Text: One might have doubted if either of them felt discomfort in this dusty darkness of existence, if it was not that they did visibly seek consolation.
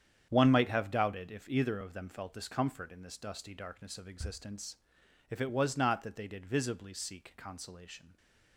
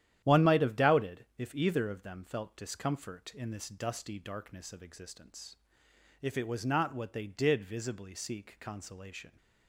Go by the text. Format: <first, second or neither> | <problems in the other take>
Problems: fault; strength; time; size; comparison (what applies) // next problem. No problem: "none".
first | starts louder than the rest; strong; until 1.3 s; 11 dB; strong in the first // says "what" for "that"; at 6.9 s